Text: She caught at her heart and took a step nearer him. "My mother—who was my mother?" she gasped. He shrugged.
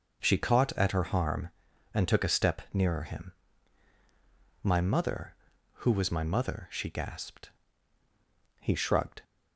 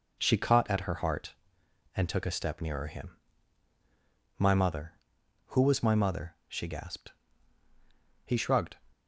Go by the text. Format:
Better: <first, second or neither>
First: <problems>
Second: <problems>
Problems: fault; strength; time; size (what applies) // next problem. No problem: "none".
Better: second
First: says "harm" for "heart"; at 1.0 s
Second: none